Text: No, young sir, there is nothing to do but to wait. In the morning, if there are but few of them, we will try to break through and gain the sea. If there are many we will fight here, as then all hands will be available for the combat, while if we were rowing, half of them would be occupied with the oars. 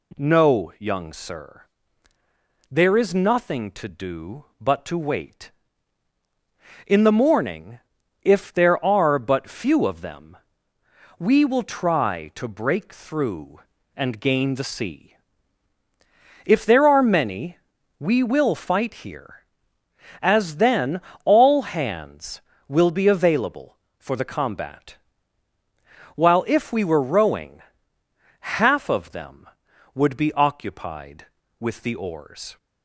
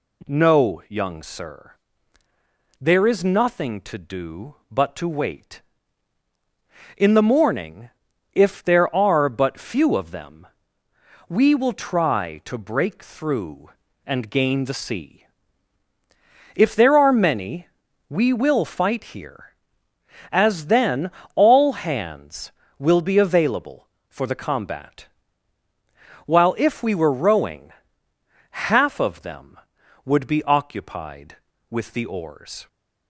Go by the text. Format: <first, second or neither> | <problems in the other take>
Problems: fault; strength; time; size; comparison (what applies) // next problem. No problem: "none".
neither | pauses between "many" and "we"; the same in both // pauses between "then" and "all"; slight; the same in both